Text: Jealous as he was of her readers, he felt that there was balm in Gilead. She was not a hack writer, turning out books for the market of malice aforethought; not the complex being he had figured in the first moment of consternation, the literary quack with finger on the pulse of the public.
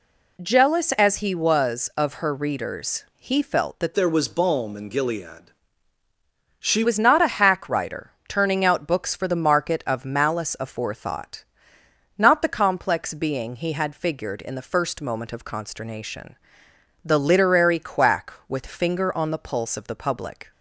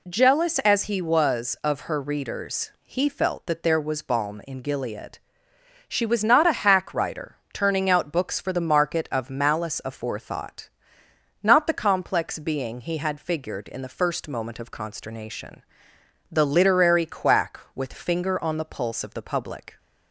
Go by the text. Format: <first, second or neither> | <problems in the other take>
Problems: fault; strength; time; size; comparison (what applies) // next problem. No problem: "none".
second | changes voice from "there" to "She"; from 3.9 to 6.8 s; 2.9 s long